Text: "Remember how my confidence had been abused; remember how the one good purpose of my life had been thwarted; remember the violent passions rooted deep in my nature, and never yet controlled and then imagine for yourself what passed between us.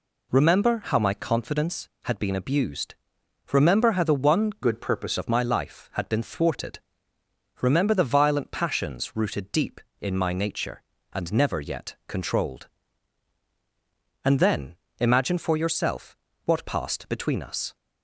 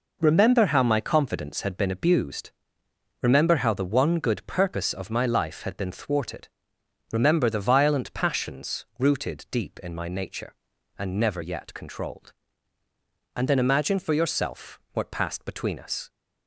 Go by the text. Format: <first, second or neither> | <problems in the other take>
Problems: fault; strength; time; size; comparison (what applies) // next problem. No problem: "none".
second | changes voice from "good" to "purpose"; from 4.6 to 5.1 s; 0.5 s long // pauses between "then" and "imagine"; slight; at 14.7 s; 0.24 s long // pauses between "yourself" and "what"; slight; at 16.1 s; 0.30 s long